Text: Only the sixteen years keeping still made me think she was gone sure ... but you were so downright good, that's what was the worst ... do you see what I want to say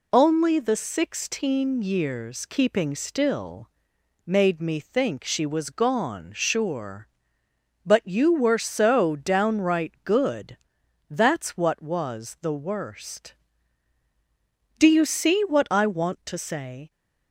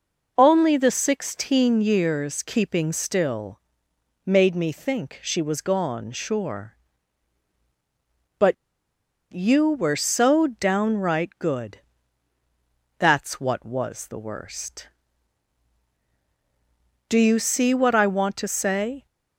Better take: first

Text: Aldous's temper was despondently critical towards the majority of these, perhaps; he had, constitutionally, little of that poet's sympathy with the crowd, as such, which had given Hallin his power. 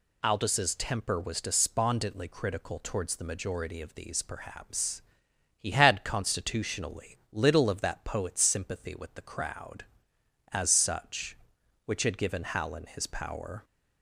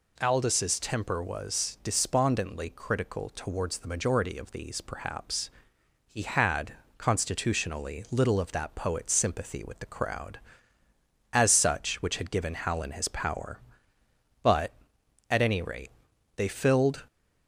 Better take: first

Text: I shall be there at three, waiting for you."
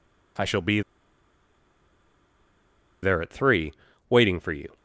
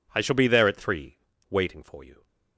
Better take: second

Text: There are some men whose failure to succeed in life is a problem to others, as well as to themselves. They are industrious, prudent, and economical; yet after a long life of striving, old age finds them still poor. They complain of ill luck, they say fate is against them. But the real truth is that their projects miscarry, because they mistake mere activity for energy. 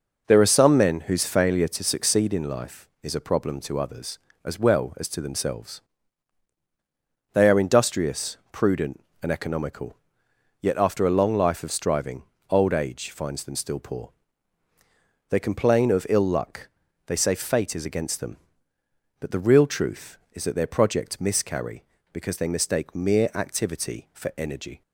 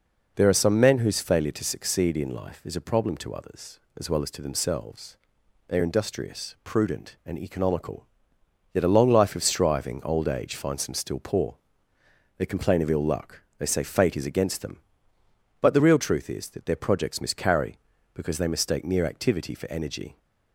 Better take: first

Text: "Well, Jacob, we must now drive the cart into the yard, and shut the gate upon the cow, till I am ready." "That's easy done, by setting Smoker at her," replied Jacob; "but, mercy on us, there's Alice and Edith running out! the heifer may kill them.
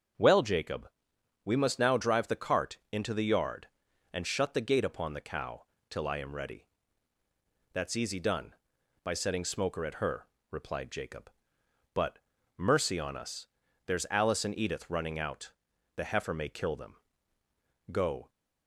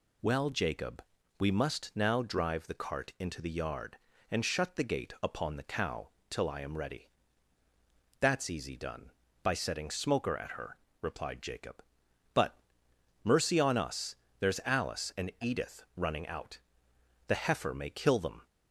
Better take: second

